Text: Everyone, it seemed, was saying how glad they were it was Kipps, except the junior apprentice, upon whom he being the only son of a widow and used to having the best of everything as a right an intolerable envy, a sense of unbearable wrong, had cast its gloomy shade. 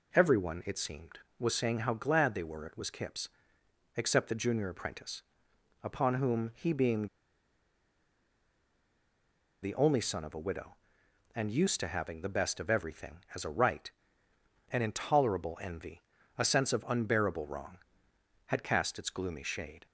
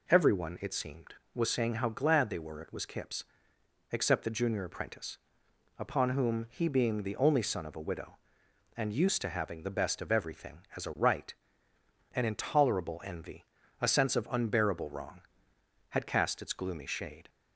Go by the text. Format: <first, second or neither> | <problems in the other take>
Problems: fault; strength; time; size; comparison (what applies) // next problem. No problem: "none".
second | pauses between "being" and "the"; strong; at 7.0 s; 2.5 s long // pauses between "right" and "an"; noticeable; at 13.8 s; 0.82 s long; noticeable in the second